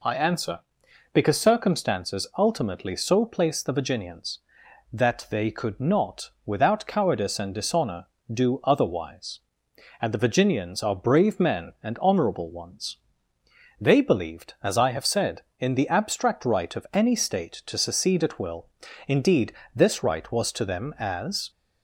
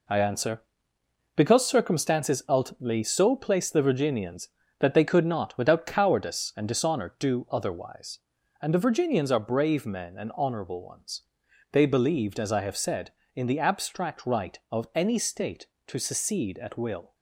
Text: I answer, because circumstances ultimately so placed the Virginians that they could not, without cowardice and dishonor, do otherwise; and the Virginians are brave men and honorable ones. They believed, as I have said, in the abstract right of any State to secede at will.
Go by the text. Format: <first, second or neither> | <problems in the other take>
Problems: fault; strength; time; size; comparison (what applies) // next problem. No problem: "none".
second | goes on to say "Indeed this right was to them as"; strong; from 19.0 s on; 2.4 s long